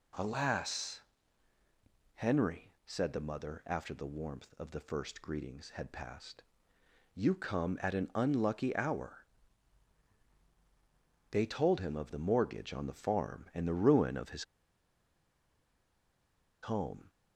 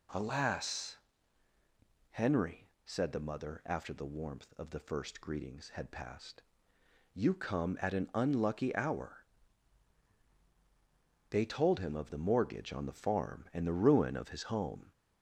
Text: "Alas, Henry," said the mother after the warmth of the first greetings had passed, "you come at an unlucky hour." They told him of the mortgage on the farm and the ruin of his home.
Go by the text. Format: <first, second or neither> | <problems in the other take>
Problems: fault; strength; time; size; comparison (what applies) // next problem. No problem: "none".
second | pauses between "his" and "home"; strong; at 14.4 s; 2.1 s long